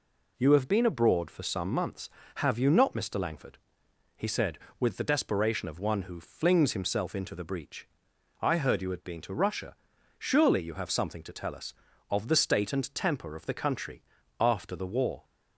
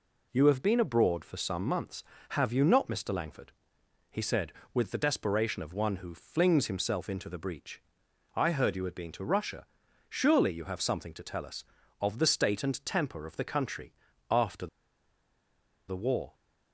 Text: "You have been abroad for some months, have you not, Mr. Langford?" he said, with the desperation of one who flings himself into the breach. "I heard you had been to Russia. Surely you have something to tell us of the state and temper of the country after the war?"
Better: first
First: pauses between "country" and "after"; slight; at 14.0 s; 0.34 s long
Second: pauses between "country" and "after"; slight; at 13.9 s; 0.34 s long // pauses between "after" and "the"; at 14.6 s; 1.2 s long

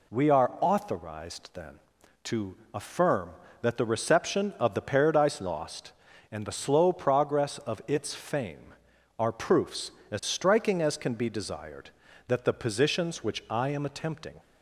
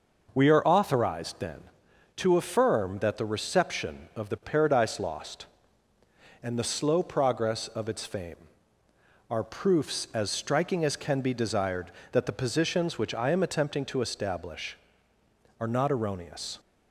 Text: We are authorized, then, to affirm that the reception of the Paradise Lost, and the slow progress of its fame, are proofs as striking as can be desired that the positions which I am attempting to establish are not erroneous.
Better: second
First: pauses between "to" and "affirm"; slight; at 2.5 s; 0.18 s long // stops before "to establish are not erroneous"; at 14.3 s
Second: none

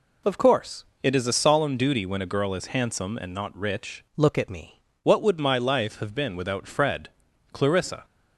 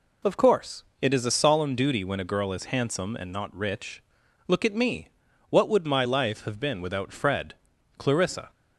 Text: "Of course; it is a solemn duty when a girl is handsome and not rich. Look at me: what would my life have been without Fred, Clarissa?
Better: second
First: changes voice from "Look" to "me"; from 4.1 to 4.8 s; 0.7 s long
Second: none

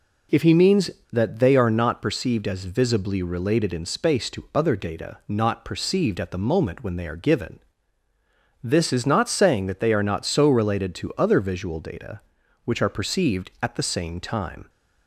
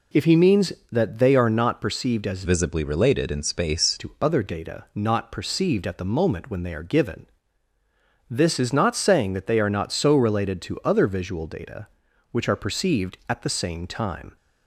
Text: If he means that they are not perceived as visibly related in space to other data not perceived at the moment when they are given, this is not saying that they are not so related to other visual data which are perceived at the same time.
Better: first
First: none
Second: changes voice from "visibly" to "space"; from 2.4 to 3.9 s; 1.5 s long

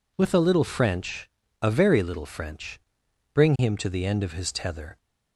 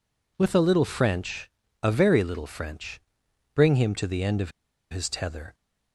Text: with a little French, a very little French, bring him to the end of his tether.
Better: first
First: none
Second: pauses between "of" and "his"; at 4.5 s; 0.40 s long

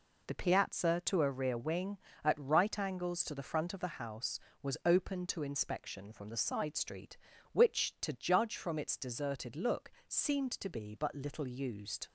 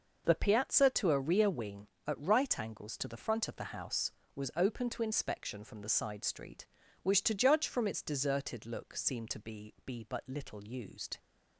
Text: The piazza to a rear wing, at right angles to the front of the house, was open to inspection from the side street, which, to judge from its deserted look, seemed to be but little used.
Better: first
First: none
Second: says "be" twice; at 9.8 s

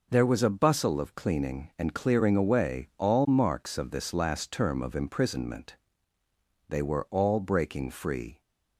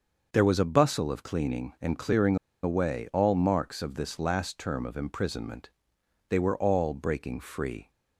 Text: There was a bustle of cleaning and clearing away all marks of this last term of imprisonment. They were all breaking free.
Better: first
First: none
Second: starts louder than the rest; until 1.3 s; 6 dB // pauses between "clearing" and "away"; slight; at 2.3 s; 0.26 s long

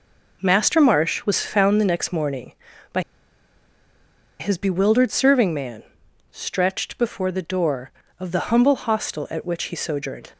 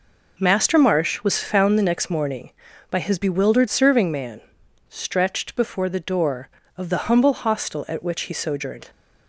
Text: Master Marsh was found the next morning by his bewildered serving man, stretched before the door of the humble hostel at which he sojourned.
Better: second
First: pauses between "by" and "his"; strong; at 3.0 s; 1.3 s long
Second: none

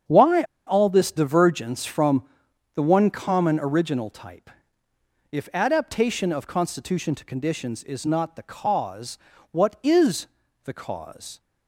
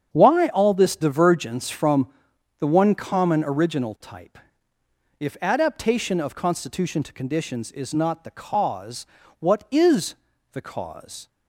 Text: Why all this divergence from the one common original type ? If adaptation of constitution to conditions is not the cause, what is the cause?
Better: second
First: starts louder than the rest; strong; until 1.3 s; 7.5 dB // pauses between "Why" and "all"; slight; at 0.4 s; 0.23 s long // pauses between "from" and "the"; noticeable; at 2.2 s; 0.52 s long // pauses between "is" and "the"; at 10.2 s; 0.38 s long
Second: starts louder than the rest; strong; until 1.1 s; 7.5 dB // pauses between "from" and "the"; noticeable; at 2.0 s; 0.52 s long // pauses between "is" and "the"; at 10.1 s; 0.38 s long

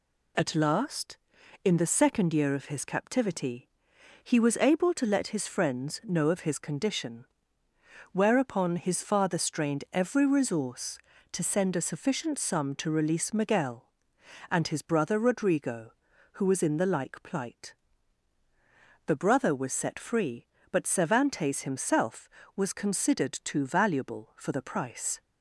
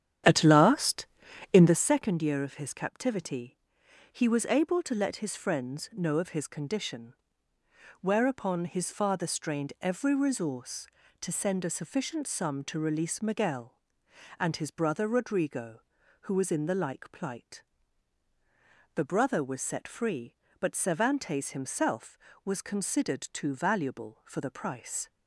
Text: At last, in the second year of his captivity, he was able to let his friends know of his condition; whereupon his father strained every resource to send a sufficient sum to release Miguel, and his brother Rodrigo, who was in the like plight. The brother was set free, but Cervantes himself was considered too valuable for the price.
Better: first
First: none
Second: starts louder than the rest; strong; until 1.9 s; 9.5 dB

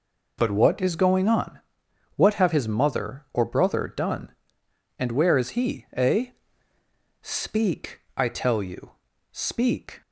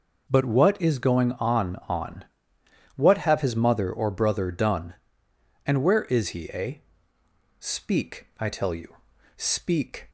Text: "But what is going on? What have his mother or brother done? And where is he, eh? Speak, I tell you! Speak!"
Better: first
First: none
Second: says "on" twice; at 1.8 s

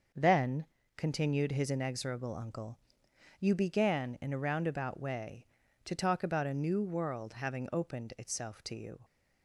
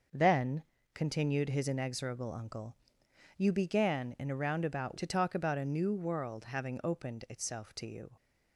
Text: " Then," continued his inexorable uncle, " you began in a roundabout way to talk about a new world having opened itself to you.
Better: first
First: none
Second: skips "way"; at 4.9 s

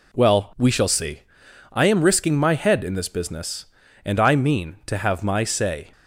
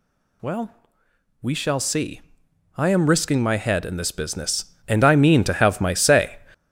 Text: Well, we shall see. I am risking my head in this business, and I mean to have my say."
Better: first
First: none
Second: gets louder; strong; throughout; 7 dB

